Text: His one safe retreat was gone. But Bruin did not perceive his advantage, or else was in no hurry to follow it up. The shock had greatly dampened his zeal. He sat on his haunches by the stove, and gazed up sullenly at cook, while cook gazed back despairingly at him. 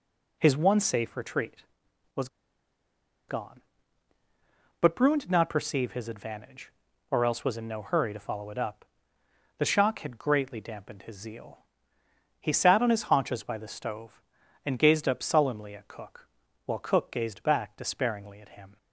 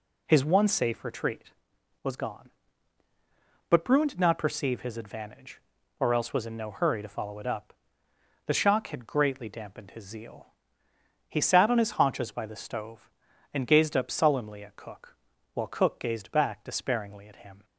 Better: second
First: pauses between "was" and "gone"; at 2.2 s; 1.0 s long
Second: none

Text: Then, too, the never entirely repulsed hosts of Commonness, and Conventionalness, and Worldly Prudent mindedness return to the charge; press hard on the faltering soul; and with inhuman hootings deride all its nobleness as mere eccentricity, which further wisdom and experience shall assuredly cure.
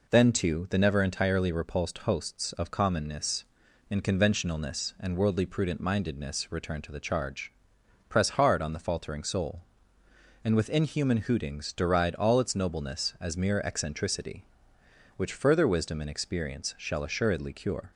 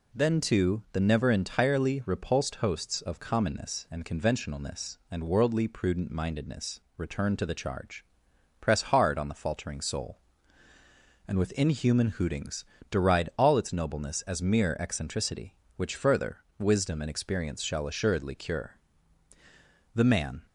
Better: first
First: none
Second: pauses between "mindedness" and "return"; slight; at 6.8 s; 0.16 s long // pauses between "hootings" and "deride"; slight; at 12.6 s; 0.24 s long // pauses between "further" and "wisdom"; slight; at 16.3 s; 0.20 s long // goes on to say "The man"; from 19.9 s on; 0.50 s long

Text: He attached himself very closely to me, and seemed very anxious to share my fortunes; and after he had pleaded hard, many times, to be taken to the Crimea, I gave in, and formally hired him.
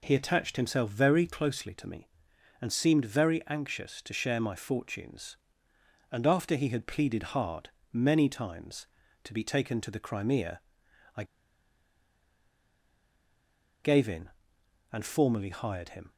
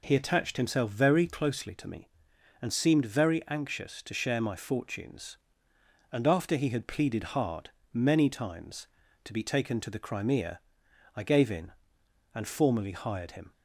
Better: second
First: pauses between "I" and "gave"; strong; at 11.2 s; 2.6 s long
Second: none

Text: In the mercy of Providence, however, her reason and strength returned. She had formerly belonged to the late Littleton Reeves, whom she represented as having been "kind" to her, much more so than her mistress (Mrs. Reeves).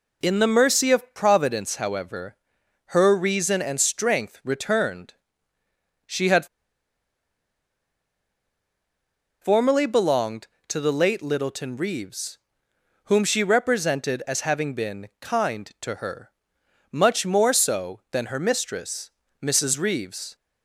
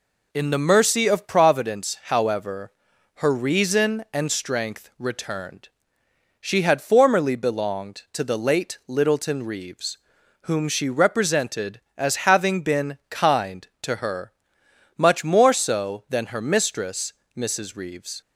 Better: second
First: pauses between "had" and "formerly"; strong; at 6.4 s; 2.9 s long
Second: none

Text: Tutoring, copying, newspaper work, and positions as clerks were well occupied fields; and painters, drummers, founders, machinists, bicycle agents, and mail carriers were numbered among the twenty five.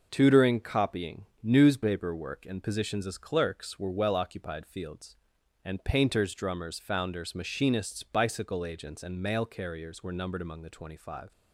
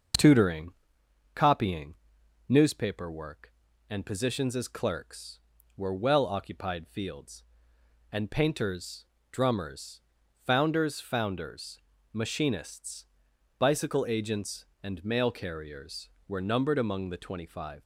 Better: first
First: none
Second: starts louder than the rest; until 1.8 s; 6 dB // says "founders" twice; at 11.0 s

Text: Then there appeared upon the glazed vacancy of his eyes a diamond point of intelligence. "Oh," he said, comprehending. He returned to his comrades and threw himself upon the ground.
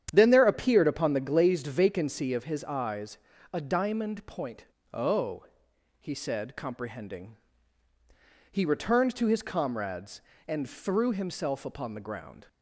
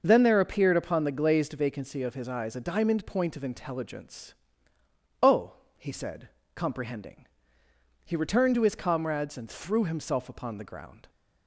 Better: second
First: starts louder than the rest; strong; until 1.1 s; 9.5 dB // pauses between "eyes" and "a"; slight; at 3.1 s; 0.36 s long // skips "of intelligence"; at 4.7 s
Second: none

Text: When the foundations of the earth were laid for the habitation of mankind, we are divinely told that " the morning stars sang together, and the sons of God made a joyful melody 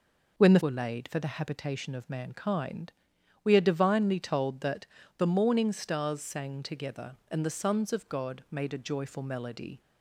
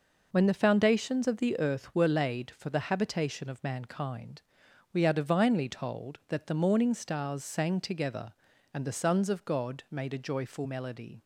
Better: second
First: skips "foundations of the earth"; at 0.6 s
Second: none

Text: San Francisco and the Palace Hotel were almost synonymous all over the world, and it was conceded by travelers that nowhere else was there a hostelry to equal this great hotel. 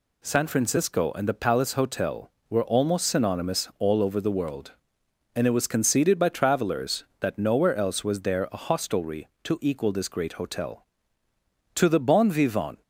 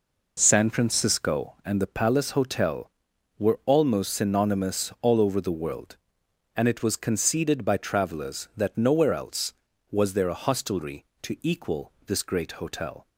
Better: second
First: goes on to say "To the bon vivant"; noticeable; from 11.7 s on; 1.0 s long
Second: none

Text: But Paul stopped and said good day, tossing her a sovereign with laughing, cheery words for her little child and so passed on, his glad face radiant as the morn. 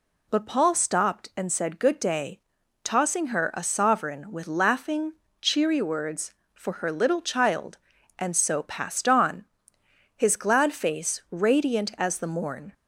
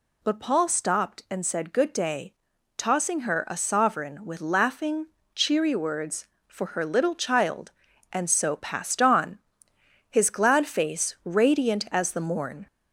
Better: first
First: none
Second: gets louder; slight; throughout; 2.5 dB

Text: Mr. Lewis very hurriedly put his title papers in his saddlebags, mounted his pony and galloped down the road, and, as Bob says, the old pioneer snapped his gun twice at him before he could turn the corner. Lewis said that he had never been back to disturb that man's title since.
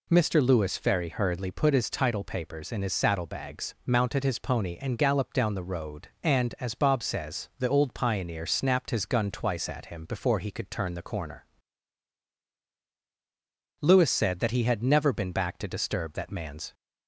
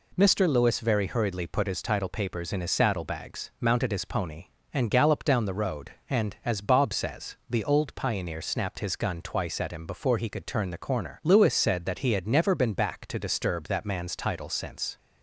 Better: second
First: stops before "title since"; at 16.7 s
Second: none

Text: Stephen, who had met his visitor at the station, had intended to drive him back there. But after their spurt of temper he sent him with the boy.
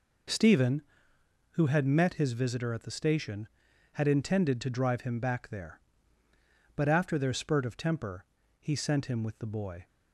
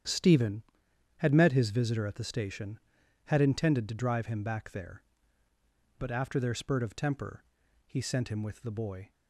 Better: first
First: pauses between "temper" and "he"; slight; at 8.2 s; 0.36 s long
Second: starts louder than the rest; strong; until 1.5 s; 9 dB // skips "who"; at 0.8 s // pauses between "temper" and "he"; noticeable; at 7.4 s; 0.46 s long

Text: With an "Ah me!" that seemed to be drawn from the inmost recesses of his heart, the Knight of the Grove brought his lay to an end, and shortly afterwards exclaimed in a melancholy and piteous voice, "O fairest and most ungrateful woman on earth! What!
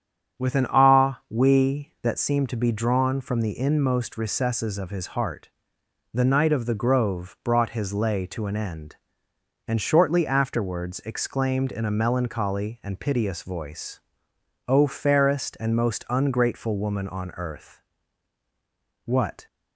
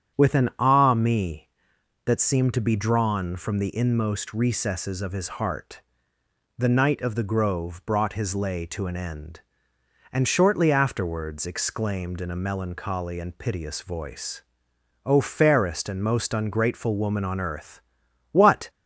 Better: second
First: starts louder than the rest; strong; until 1.4 s; 8.5 dB // says "we" for "me"; at 1.2 s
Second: starts louder than the rest; strong; until 1.2 s; 9 dB

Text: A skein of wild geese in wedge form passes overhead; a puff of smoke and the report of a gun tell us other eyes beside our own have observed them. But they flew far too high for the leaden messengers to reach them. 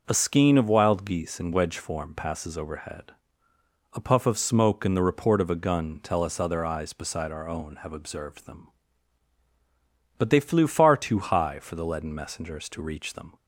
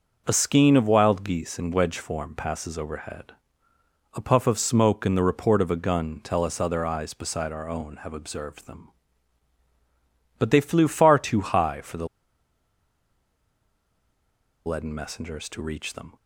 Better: first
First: none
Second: pauses between "the" and "leaden"; strong; at 12.0 s; 2.5 s long

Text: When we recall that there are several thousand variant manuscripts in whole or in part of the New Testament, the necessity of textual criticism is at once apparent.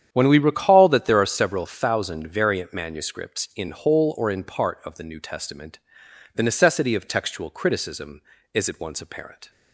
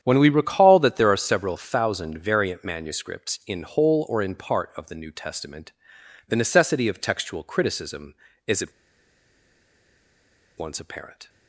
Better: first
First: starts louder than the rest; strong; until 1.1 s; 9 dB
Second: starts louder than the rest; strong; until 1.0 s; 9 dB // pauses between "at" and "once"; strong; at 8.7 s; 1.8 s long

